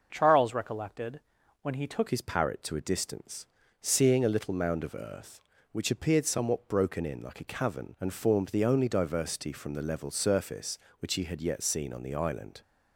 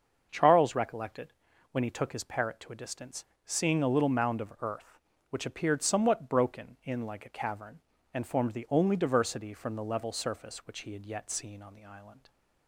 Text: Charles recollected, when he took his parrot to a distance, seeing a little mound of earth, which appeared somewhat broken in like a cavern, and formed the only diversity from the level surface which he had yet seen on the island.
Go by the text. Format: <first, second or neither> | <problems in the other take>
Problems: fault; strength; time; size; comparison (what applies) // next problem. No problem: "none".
second | starts louder than the rest; noticeable; until 1.1 s; 6 dB; also in the second // changes voice at "his"; from 2.1 s on; 10.5 s long